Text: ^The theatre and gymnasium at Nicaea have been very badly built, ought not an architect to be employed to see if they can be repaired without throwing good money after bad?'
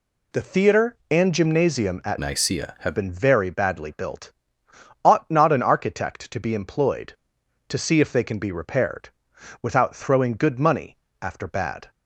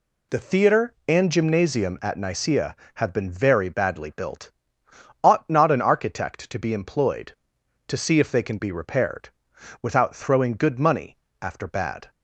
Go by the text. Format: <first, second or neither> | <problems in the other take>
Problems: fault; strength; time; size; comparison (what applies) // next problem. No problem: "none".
second | changes voice from "Nicaea" to "have"; from 2.1 to 2.9 s; 0.8 s long // pauses between "repaired" and "without"; noticeable; at 9.0 s; 0.52 s long; noticeable in the second // pauses between "money" and "after"; slight; at 10.9 s; 0.26 s long; slight in the second